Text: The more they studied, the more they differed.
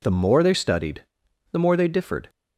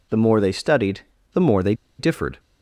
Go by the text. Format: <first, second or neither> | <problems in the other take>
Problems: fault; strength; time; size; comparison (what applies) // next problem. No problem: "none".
first | pauses between "they" and "differed"; slight; at 1.7 s; 0.25 s long